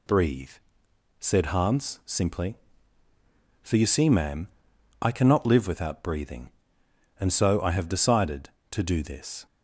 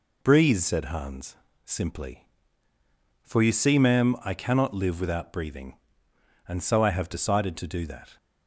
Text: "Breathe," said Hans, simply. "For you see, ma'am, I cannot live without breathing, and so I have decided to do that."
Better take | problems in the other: second | says "this" for "that"; at 9.0 s

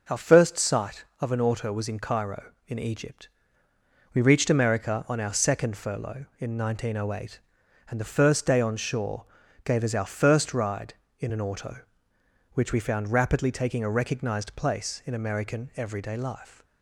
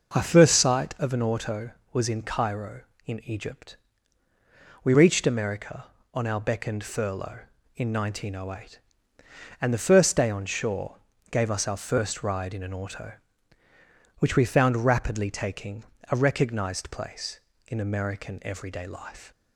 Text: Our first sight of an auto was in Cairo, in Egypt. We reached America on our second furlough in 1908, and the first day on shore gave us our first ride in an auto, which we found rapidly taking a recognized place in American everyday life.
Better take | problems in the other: first | says "beckoned" for "second"; at 6.4 s // pauses between "shore" and "gave"; slight; at 10.9 s; 0.34 s long; also in the first // pauses between "taking" and "a"; slight; at 15.8 s; 0.26 s long

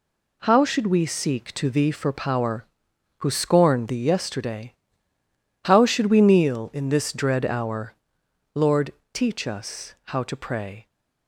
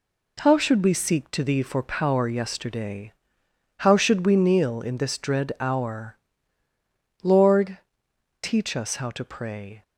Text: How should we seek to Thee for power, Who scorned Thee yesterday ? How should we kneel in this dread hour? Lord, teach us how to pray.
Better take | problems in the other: first | skips "Who scorned Thee"; at 2.2 s

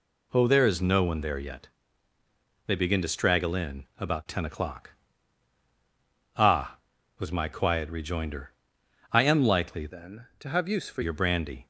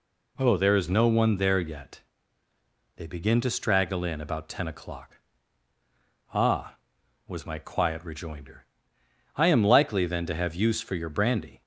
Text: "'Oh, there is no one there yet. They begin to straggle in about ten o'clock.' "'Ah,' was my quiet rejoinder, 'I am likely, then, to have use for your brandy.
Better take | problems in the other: second | changes voice from "then" to "for"; from 9.8 to 11.0 s; 1.2 s long

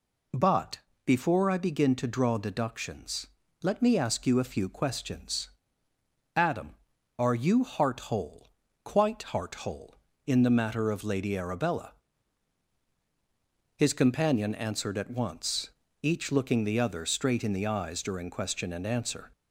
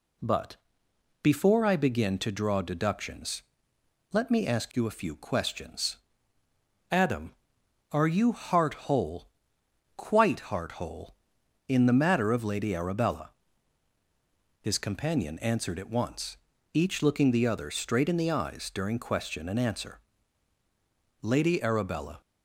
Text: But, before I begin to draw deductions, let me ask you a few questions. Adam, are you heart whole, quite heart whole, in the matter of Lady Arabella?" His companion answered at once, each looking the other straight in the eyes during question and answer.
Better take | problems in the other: first | goes on to say "Lady Arabella"; noticeable; from 21.2 s on; 0.98 s long

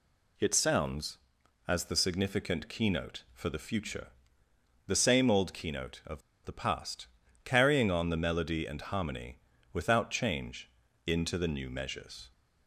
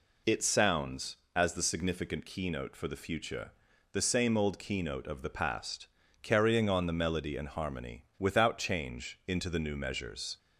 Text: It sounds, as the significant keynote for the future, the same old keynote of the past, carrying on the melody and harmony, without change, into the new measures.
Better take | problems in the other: second | pauses between "of" and "the"; slight; at 6.2 s; 0.24 s long

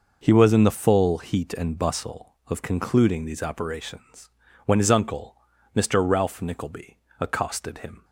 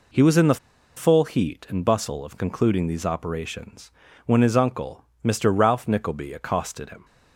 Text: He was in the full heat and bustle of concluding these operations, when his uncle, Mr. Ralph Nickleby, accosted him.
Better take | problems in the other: first | pauses between "the" and "full"; at 0.5 s; 0.39 s long

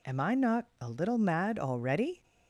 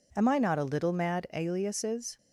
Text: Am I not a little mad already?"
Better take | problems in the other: first | says "aliases" for "already"; at 1.3 s

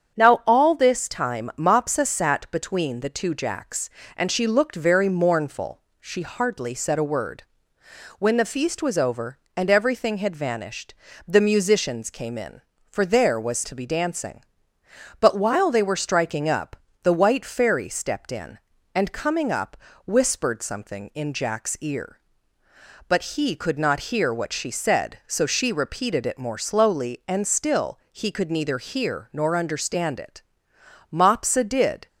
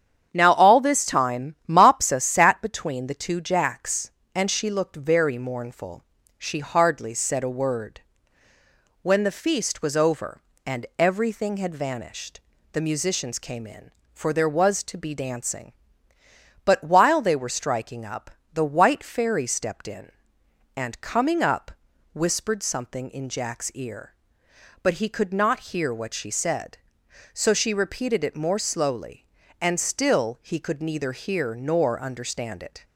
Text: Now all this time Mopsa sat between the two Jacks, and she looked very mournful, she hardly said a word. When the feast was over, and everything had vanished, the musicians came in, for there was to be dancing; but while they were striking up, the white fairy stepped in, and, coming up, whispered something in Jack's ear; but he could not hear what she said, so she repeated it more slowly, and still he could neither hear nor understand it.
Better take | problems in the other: second | starts louder than the rest; strong; until 1.2 s; 8 dB; strong in the second // pauses between "still" and "he"; slight; at 27.9 s; 0.16 s long // goes on to say "Mopsa did"; noticeable; from 31.1 s on; 0.96 s long

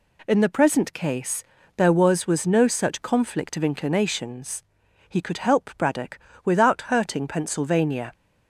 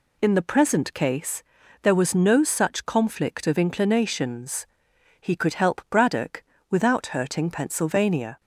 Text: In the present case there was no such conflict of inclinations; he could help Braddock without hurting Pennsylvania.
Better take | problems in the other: second | pauses between "case" and "there"; slight; at 1.4 s; 0.34 s long; also in the second // says "was" twice; at 2.2 s // pauses between "Braddock" and "without"; slight; at 6.1 s; 0.26 s long; slight in the second

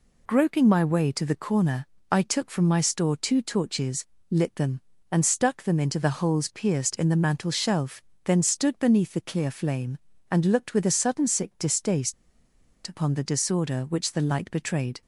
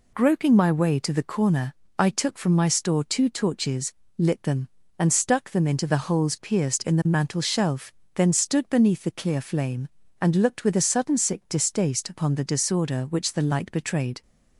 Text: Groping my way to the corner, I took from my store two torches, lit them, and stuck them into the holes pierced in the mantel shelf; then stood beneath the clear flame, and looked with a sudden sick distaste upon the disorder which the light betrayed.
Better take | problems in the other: second | pauses between "distaste" and "upon"; noticeable; at 12.1 s; 0.72 s long

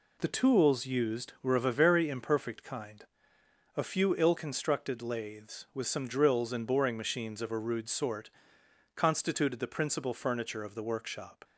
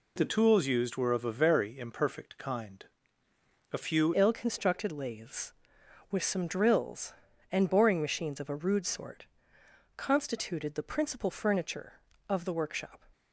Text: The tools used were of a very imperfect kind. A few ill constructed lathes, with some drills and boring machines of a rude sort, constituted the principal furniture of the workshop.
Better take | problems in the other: first | changes voice at "ill"; from 4.1 s on; 8.9 s long

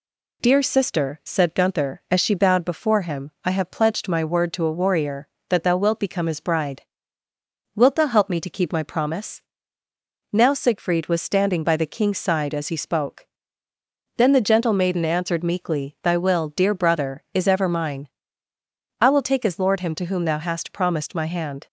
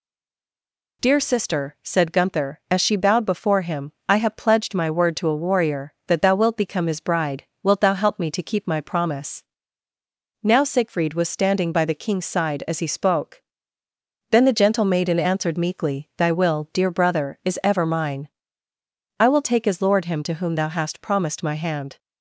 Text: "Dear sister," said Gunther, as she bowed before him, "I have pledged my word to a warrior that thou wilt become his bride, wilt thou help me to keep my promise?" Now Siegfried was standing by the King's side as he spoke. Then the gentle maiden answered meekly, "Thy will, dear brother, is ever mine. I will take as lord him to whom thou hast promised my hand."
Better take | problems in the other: first | stays silent before the first word; until 1.0 s; 1.0 s long

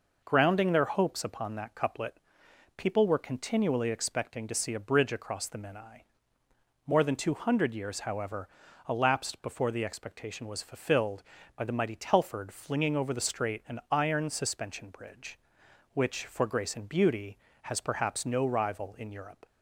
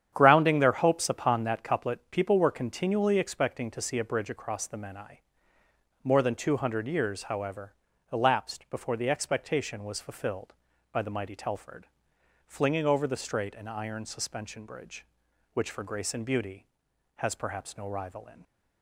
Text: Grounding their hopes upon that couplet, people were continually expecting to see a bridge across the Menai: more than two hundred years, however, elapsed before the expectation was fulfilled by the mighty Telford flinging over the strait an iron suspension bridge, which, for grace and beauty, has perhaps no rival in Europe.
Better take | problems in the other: first | starts louder than the rest; strong; until 1.1 s; 9.5 dB // pauses between "Telford" and "flinging"; noticeable; at 11.8 s; 0.60 s long // stops before "Europe"; at 18.4 s

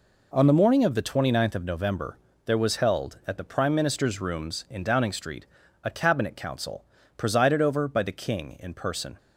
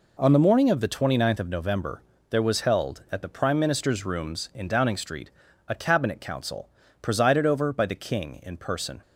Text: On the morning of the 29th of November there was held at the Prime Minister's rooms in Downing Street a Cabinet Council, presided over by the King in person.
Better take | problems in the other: neither | pauses between "November" and "there"; slight; the same in both // pauses between "Street" and "a"; the same in both

